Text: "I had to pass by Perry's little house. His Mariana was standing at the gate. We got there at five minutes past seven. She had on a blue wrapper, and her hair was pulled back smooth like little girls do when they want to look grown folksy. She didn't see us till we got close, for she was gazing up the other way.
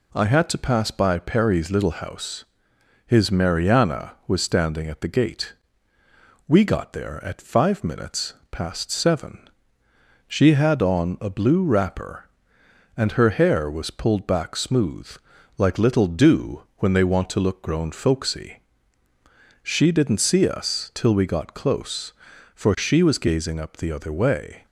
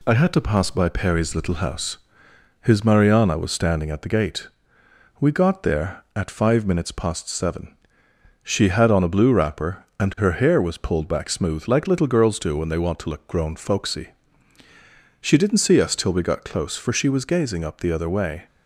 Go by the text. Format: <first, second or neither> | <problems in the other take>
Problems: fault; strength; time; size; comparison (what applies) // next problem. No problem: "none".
second | pauses between "minutes" and "past"; slight; at 8.3 s; 0.18 s long // pauses between "smooth" and "like"; noticeable; at 15.0 s; 0.48 s long // skips "girls"; at 16.0 s